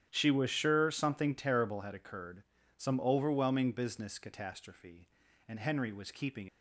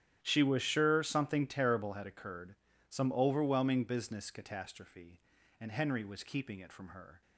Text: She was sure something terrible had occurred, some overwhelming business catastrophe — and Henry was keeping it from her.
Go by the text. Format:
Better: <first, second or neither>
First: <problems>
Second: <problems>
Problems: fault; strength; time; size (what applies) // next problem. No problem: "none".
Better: second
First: starts louder than the rest; strong; until 1.1 s; 10 dB // stops before "it from her"; at 6.4 s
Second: starts louder than the rest; strong; until 1.2 s; 11 dB